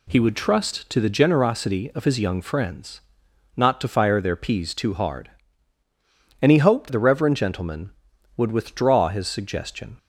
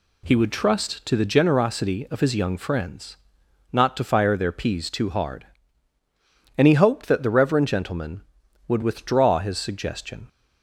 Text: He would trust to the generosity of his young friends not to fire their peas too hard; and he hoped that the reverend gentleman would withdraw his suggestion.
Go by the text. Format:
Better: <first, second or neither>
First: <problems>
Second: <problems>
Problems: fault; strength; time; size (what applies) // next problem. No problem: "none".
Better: second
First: pauses between "friends" and "not"; noticeable; at 3.0 s; 0.54 s long // skips "that"; at 6.9 s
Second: pauses between "friends" and "not"; noticeable; at 3.1 s; 0.54 s long